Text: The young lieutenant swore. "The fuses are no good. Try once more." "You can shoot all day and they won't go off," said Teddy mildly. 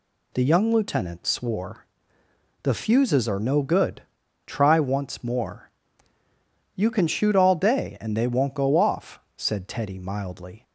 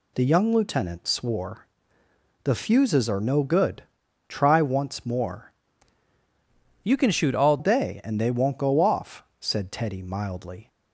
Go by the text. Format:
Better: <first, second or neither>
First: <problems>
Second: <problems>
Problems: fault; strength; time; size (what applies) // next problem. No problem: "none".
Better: first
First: none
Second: changes voice from "You" to "all"; from 6.8 to 7.5 s; 0.7 s long